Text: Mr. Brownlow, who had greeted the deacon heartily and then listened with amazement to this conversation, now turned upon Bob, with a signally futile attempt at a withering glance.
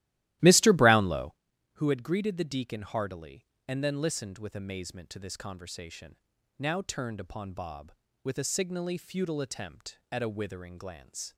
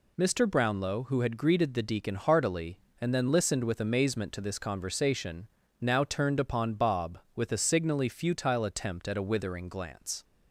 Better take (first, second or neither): second